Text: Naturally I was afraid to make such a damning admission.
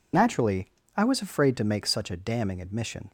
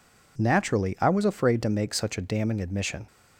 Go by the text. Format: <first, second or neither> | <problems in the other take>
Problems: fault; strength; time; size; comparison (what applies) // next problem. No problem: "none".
second | loses the start of "Naturally"; at 0.1 s; 45 ms // pauses between "Naturally" and "I"; slight; at 0.6 s; 0.26 s long